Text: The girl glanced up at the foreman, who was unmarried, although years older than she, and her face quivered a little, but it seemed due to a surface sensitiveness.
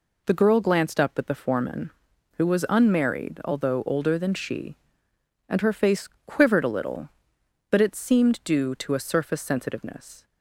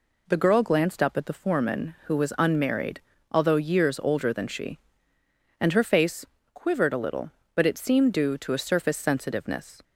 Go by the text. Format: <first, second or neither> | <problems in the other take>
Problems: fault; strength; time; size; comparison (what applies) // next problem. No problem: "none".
second | skips "years"; at 3.8 s // pauses between "face" and "quivered"; slight; at 6.0 s; 0.18 s long; slight in the second